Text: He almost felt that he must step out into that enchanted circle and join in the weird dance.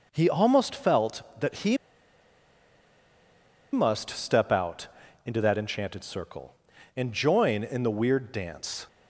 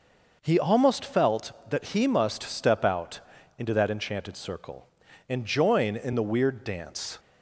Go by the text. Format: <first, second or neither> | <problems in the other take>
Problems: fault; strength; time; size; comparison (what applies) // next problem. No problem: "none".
second | pauses between "he" and "must"; strong; at 1.7 s; 1.9 s long // pauses between "out" and "into"; at 4.8 s; 0.38 s long; also in the second